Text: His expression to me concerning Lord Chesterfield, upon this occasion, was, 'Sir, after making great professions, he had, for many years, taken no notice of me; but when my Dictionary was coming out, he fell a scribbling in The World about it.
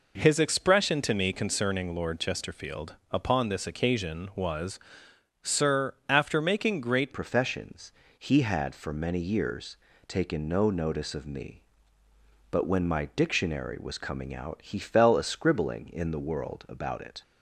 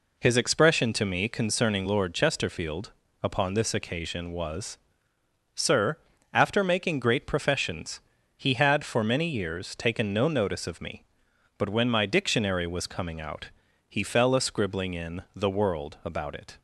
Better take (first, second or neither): second